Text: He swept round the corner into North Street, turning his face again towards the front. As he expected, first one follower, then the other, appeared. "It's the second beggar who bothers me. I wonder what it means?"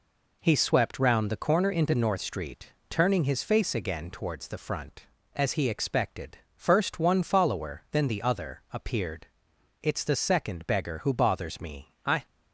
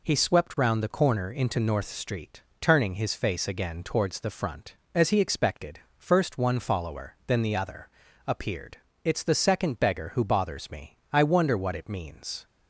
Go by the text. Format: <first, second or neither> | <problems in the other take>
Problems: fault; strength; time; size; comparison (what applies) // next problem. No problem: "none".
second | stops before "wonder what it means"; at 12.2 s